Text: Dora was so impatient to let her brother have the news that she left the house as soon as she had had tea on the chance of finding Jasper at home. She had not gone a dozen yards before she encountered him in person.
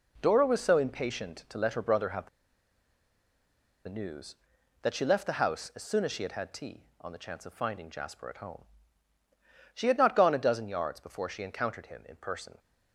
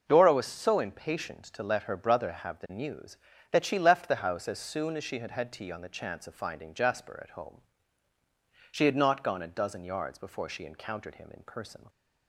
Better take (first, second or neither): second